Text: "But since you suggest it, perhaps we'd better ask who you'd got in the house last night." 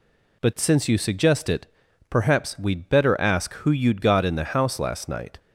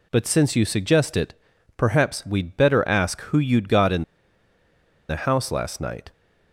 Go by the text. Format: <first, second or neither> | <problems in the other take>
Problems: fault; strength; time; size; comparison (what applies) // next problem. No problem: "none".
first | pauses between "in" and "the"; at 4.0 s; 1.0 s long